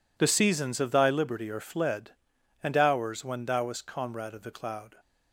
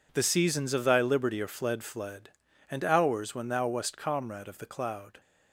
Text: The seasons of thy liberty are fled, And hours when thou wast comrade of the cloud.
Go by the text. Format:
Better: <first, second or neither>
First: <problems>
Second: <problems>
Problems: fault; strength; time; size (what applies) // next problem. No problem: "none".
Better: first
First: none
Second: says "fled" twice; at 1.8 s